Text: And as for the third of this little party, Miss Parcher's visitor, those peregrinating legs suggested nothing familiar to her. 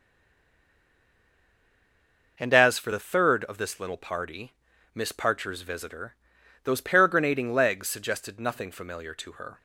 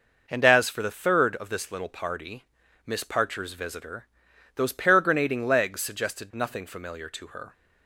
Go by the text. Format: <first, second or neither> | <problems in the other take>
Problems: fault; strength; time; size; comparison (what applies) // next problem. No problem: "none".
second | stays silent before the first word; until 2.3 s; 2.3 s long